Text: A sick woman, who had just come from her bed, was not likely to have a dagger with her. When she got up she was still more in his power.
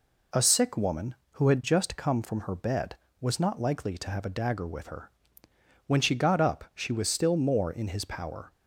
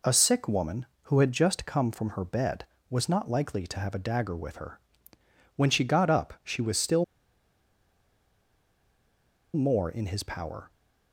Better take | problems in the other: first | pauses between "still" and "more"; strong; at 7.0 s; 2.5 s long

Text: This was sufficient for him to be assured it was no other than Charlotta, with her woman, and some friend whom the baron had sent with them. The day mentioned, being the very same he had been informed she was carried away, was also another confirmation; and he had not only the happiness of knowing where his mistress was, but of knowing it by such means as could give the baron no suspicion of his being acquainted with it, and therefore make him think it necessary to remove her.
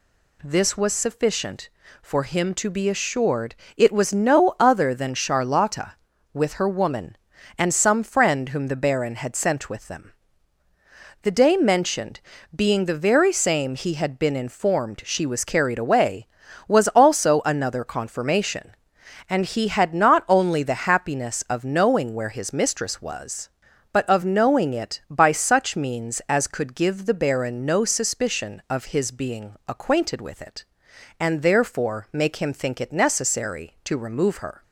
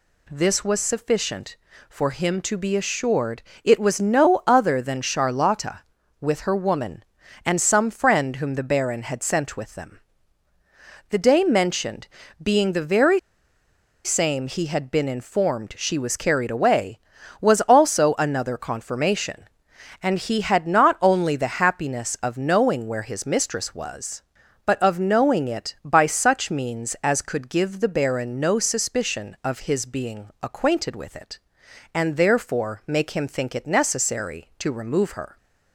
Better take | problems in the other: first | pauses between "assured" and "it"; slight; at 3.4 s; 0.22 s long; slight in the first // pauses between "very" and "same"; noticeable; at 13.1 s; 0.85 s long

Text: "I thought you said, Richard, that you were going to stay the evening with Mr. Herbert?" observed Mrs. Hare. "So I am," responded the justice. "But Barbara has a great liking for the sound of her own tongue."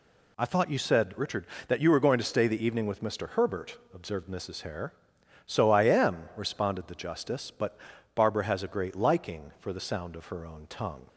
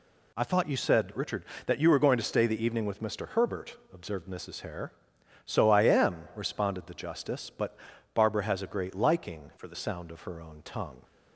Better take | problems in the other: first | pauses between "But" and "Barbara"; at 7.7 s; 0.38 s long; also in the first // changes voice from "for" to "the"; from 9.5 to 9.7 s; 0.2 s long

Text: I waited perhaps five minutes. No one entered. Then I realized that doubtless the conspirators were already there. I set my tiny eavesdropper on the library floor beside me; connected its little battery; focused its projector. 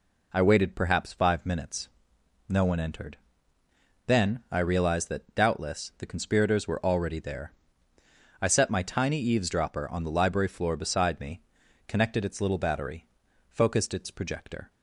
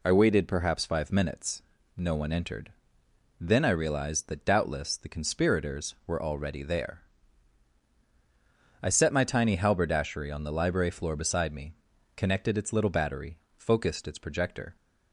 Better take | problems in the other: first | says "halberdashery" for "eavesdropper"; at 9.5 s

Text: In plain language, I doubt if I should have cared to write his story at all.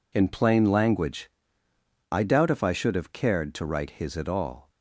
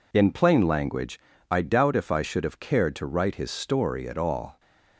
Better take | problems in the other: second | skips "story"; at 4.1 s

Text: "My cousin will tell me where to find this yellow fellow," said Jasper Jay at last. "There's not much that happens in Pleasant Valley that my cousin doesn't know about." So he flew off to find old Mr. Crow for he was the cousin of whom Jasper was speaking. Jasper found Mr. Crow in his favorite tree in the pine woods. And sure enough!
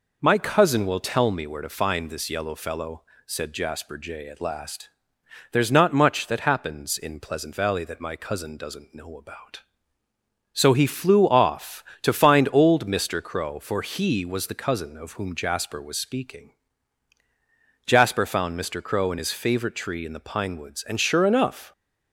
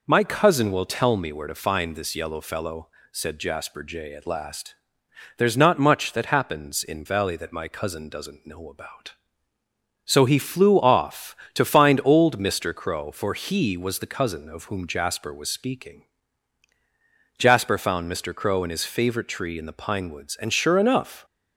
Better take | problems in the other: first | skips "Pleasant"; at 7.0 s

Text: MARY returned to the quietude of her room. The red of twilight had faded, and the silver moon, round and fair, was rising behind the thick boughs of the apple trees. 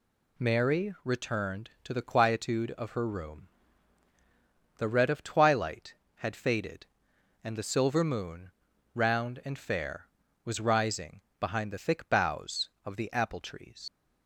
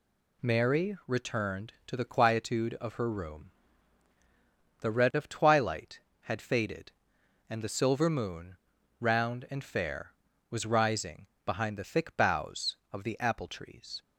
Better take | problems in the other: second | pauses between "rising" and "behind"; slight; at 11.2 s; 0.18 s long; slight in the second // leaves "trees" unfinished; at 13.8 s; 65 ms

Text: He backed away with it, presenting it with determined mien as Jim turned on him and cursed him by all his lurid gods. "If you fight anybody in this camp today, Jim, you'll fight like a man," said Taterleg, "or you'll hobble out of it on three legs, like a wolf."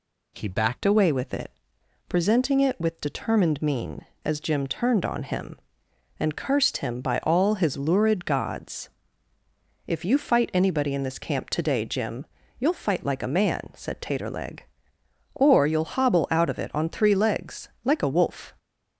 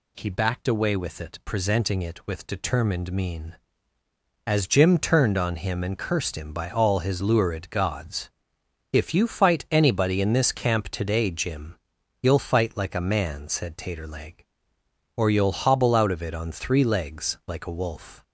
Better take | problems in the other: second | changes voice at "away"; from 0.8 s on; 17.7 s long

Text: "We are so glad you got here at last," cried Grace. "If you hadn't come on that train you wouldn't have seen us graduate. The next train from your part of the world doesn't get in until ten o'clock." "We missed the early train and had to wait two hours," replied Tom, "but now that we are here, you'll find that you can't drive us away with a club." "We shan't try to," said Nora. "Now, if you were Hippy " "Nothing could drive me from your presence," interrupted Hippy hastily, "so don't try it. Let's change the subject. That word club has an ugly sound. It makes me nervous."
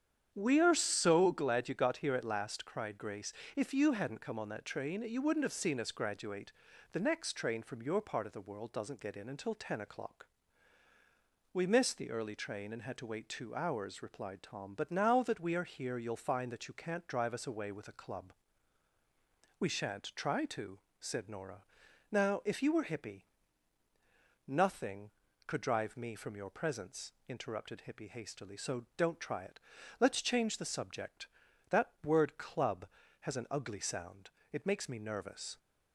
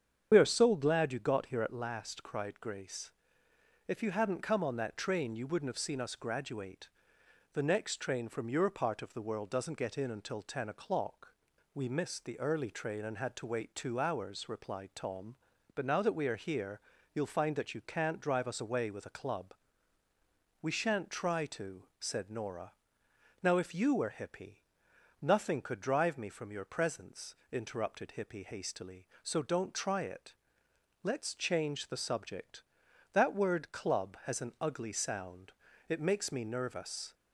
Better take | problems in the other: first | loses the start of "We"; at 0.3 s; 40 ms // starts louder than the rest; strong; until 1.3 s; 8 dB; strong in the first

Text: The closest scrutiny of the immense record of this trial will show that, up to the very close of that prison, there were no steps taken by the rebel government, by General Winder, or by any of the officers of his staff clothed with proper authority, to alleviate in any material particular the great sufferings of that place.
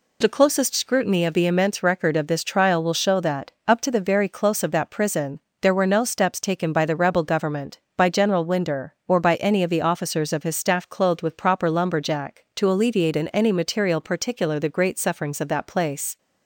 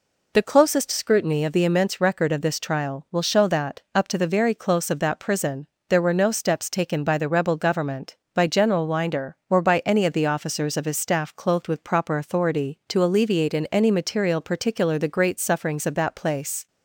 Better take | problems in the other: second | says "lumberjack" for "authority"; at 11.7 s

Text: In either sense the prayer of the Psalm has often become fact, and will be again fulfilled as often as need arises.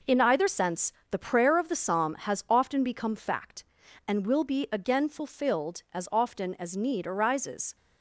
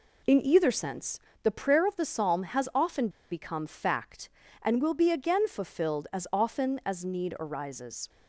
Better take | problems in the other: first | pauses between "sense" and "the"; slight; at 1.1 s; 0.24 s long; slight in the first // pauses between "often" and "become"; slight; at 3.0 s; 0.22 s long

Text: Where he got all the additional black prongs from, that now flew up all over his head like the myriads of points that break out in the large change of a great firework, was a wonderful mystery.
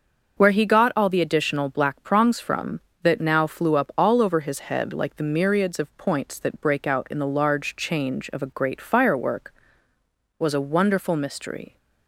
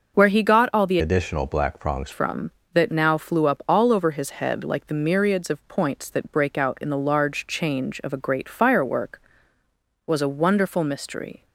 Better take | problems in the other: first | starts louder than the rest; until 1.2 s; 6.5 dB; also in the first // changes voice from "additional" to "prongs"; from 0.9 to 2.1 s; 1.2 s long

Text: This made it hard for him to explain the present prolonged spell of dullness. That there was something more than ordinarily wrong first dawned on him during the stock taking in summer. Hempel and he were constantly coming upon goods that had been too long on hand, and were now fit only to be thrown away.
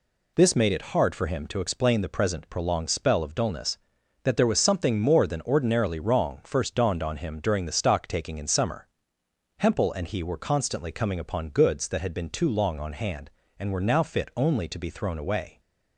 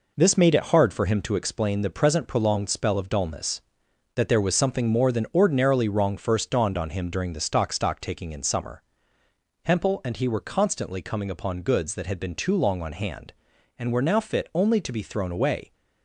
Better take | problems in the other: first | says "stock" twice; at 7.7 s

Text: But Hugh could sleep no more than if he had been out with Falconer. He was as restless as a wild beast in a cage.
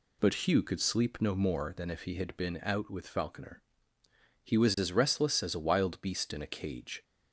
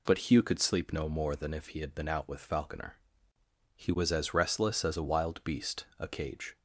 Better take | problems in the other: first | skips "in"; at 5.9 s

